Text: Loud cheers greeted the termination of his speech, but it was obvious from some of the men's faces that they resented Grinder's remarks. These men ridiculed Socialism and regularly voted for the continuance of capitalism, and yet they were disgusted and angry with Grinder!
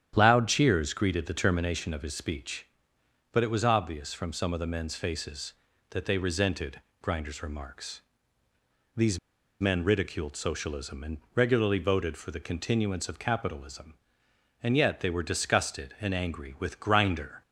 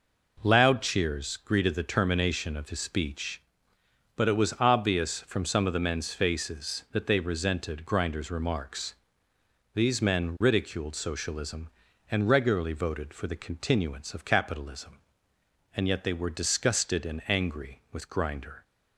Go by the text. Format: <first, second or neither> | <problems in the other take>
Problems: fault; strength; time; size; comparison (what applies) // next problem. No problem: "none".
second | starts louder than the rest; strong; until 1.1 s; 9.5 dB // pauses between "resented" and "Grinder's"; slight; at 6.8 s; 0.22 s long // pauses between "These" and "men"; at 9.1 s; 0.42 s long // pauses between "and" and "regularly"; slight; at 11.1 s; 0.16 s long